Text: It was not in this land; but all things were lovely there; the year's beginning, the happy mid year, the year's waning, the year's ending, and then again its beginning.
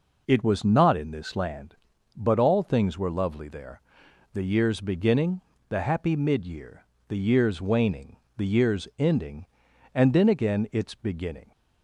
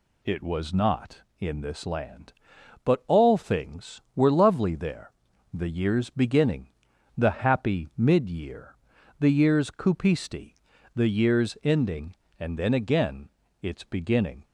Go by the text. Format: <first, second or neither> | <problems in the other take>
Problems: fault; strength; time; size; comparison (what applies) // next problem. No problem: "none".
first | says "cupisti" for "waning"; at 9.6 s // pauses between "again" and "its"; slight; at 13.2 s; 0.32 s long